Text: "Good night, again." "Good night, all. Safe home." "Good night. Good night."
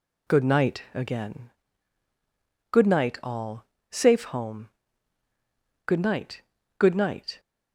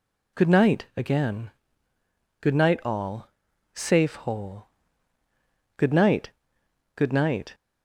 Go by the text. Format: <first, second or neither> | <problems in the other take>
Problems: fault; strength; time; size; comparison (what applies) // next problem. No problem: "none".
first | says "hole" for "home"; at 4.1 s